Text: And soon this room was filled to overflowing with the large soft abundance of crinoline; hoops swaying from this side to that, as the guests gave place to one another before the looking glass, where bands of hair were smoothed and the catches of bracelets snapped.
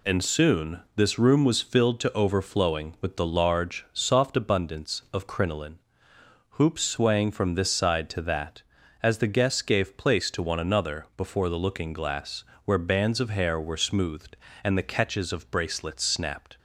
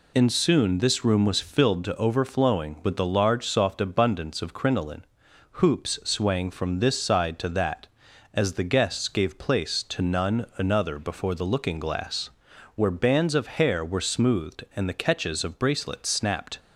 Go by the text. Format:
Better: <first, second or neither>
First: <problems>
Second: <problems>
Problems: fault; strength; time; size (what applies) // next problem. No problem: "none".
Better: first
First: none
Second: says "none" for "one"; at 10.0 s